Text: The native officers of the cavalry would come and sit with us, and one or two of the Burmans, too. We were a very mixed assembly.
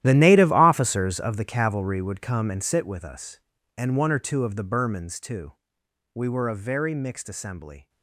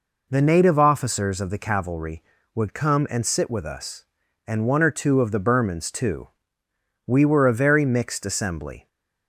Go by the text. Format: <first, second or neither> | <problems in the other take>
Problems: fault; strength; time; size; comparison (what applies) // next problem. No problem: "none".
second | gets quieter; strong; throughout; 15.5 dB